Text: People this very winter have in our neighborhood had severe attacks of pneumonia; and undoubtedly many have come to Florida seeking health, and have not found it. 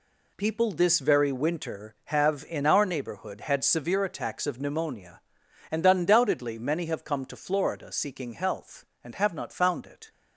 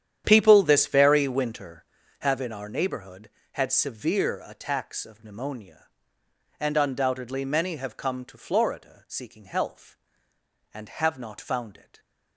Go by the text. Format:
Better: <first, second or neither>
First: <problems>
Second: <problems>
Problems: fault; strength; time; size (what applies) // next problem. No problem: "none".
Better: first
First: none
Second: starts louder than the rest; strong; until 2.2 s; 9.5 dB